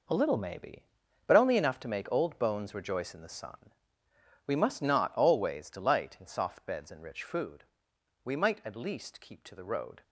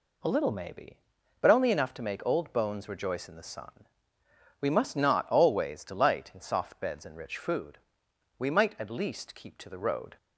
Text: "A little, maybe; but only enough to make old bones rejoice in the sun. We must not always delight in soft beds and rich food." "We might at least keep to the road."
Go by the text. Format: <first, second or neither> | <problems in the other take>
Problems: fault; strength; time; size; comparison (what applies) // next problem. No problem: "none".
second | gets quieter; strong; throughout; 11 dB